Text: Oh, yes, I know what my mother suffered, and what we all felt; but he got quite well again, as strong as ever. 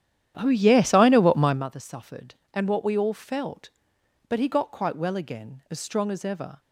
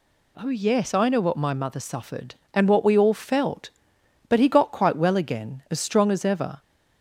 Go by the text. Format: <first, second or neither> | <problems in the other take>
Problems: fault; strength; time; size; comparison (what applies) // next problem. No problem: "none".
second | starts louder than the rest; strong; until 1.7 s; 10.5 dB